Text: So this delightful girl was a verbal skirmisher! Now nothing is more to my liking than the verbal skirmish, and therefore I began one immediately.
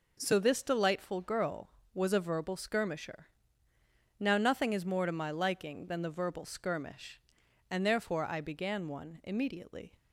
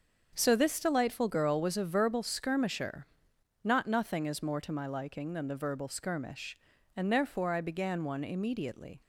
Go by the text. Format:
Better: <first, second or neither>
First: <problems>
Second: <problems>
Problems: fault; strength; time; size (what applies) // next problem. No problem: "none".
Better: first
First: none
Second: starts louder than the rest; until 1.3 s; 6.5 dB // says "Not" for "Now"; at 3.6 s